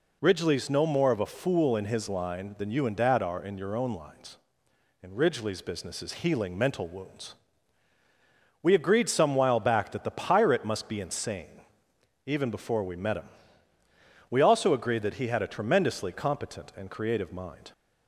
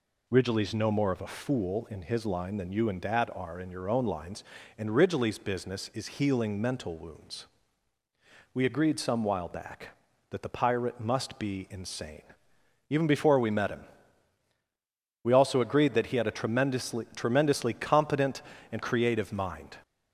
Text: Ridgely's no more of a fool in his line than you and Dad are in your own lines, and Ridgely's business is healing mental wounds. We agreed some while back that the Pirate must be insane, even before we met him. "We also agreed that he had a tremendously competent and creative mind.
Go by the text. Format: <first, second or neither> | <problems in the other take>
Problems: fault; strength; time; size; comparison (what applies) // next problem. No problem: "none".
first | says "tremendously" twice; at 17.1 s